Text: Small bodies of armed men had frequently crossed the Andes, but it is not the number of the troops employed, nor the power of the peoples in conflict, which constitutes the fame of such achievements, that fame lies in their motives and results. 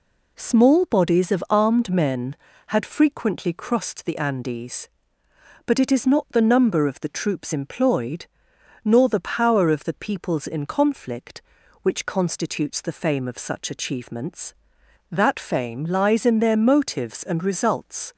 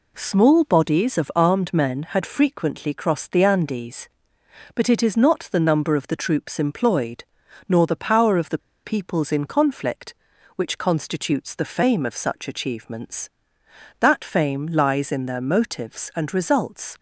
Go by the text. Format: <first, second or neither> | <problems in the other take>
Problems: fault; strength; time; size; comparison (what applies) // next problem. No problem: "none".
first | pauses between "the" and "peoples"; slight; at 8.5 s; 0.26 s long